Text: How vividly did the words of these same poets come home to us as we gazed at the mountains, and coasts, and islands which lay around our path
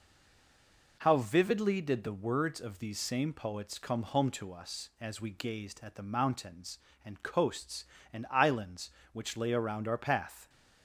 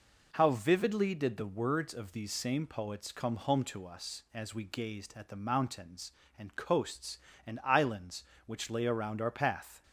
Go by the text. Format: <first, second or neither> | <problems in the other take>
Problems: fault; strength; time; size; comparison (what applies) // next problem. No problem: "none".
second | stays silent before the first word; until 0.9 s; 0.9 s long